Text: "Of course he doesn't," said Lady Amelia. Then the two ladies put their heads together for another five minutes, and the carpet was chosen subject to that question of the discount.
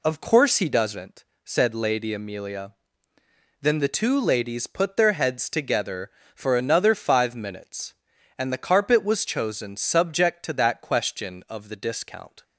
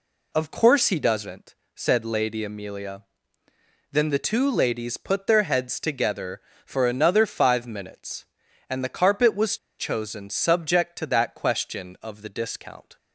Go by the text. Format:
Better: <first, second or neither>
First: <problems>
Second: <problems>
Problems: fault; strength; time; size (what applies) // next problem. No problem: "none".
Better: first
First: none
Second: pauses between "was" and "chosen"; slight; at 9.5 s; 0.20 s long